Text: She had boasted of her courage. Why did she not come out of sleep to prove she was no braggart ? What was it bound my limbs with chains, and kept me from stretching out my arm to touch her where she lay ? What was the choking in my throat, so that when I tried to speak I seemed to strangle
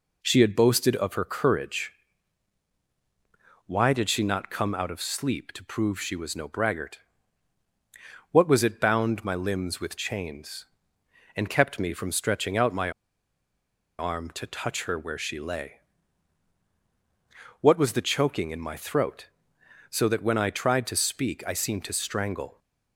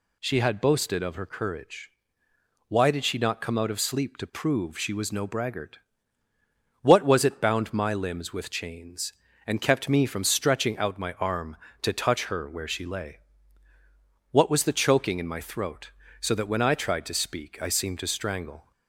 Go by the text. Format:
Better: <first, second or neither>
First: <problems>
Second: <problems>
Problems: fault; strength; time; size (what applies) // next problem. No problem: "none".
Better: second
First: pauses between "my" and "arm"; at 12.9 s; 1.0 s long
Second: none